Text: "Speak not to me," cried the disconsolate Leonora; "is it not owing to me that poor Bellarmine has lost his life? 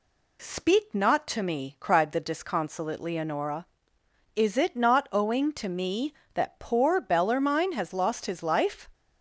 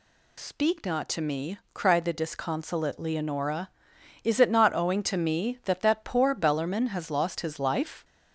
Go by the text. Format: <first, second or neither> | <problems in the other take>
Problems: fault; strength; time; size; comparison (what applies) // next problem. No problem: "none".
first | says "that" twice; at 5.8 s